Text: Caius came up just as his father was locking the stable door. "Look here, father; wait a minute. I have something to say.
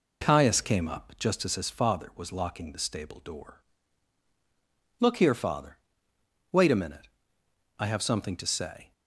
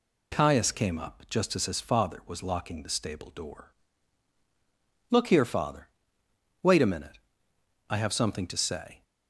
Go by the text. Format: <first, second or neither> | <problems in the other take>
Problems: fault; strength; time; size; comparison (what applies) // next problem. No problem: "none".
second | starts louder than the rest; until 1.5 s; 3.5 dB